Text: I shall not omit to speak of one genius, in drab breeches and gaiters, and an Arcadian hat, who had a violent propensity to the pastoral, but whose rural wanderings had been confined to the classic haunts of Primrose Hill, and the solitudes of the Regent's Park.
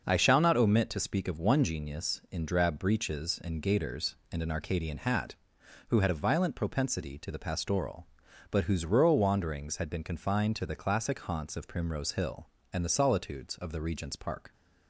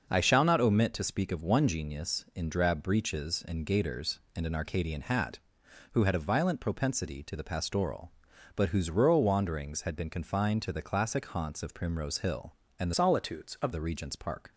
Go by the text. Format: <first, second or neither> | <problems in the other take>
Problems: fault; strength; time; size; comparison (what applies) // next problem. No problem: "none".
first | starts louder than the rest; noticeable; until 1.1 s; 6 dB; noticeable in the first // changes voice from "solitudes" to "of"; from 12.9 to 13.7 s; 0.8 s long